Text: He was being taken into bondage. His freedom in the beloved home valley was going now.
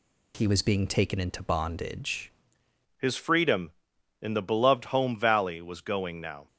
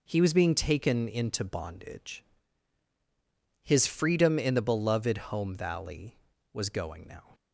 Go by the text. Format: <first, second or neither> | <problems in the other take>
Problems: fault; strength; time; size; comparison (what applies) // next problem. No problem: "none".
second | changes voice at "His"; from 2.9 s on; 3.5 s long